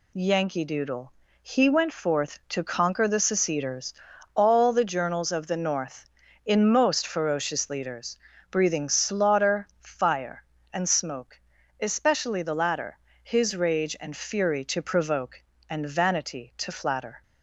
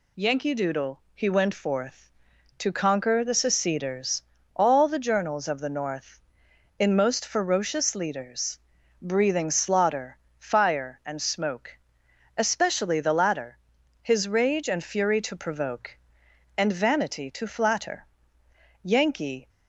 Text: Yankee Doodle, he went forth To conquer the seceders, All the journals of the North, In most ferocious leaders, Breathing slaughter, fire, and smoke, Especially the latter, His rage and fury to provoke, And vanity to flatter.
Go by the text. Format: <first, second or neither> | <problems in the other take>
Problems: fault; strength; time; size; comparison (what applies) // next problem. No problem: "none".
first | goes on to say "Yankee"; noticeable; from 18.8 s on; 0.66 s long